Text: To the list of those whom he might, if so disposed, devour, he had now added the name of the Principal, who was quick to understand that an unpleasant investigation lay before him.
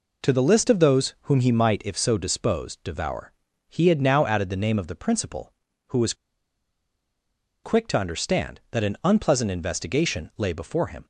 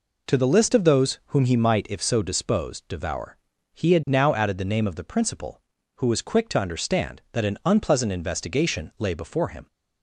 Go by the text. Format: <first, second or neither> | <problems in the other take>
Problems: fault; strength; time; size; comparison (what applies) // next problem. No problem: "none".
second | pauses between "was" and "quick"; strong; at 6.1 s; 1.5 s long